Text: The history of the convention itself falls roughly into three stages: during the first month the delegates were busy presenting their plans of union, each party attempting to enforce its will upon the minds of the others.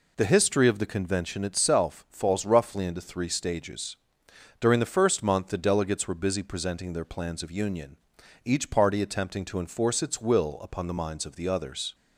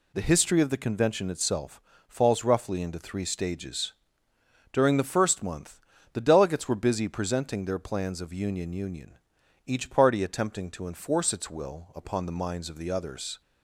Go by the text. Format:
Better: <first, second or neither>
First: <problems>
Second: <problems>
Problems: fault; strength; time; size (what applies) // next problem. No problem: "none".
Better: first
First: none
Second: pauses between "itself" and "falls"; slight; at 1.8 s; 0.28 s long // pauses between "month" and "the"; slight; at 5.8 s; 0.32 s long // says "union" twice; at 8.7 s